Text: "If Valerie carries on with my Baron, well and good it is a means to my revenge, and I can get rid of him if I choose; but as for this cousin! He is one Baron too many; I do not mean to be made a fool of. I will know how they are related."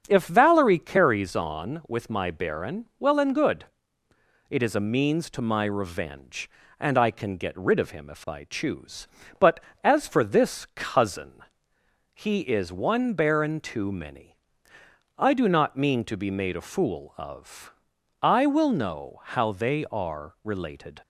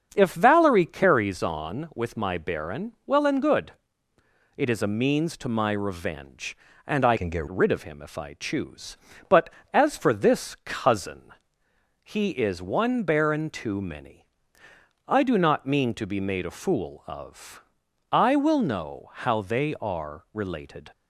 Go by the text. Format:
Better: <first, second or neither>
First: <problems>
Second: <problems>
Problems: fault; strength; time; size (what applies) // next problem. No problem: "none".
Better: first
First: starts louder than the rest; strong; until 1.0 s; 7.5 dB // pauses between "good" and "it"; noticeable; at 3.6 s; 0.86 s long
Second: starts louder than the rest; until 1.1 s; 7 dB // pauses between "good" and "it"; noticeable; at 3.7 s; 0.86 s long // changes voice from "can" to "get"; from 7.1 to 7.4 s; 0.3 s long